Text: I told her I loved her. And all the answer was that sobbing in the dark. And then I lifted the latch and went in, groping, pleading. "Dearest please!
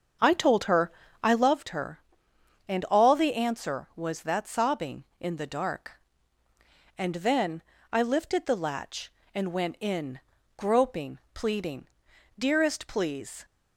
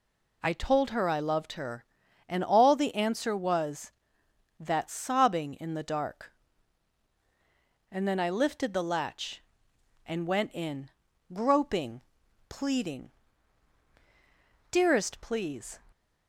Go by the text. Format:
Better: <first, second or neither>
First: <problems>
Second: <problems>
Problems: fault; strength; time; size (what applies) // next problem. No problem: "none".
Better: second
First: starts louder than the rest; until 1.6 s; 7 dB // pauses between "her" and "I"; slight; at 0.9 s; 0.32 s long // pauses between "then" and "I"; slight; at 7.6 s; 0.28 s long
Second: none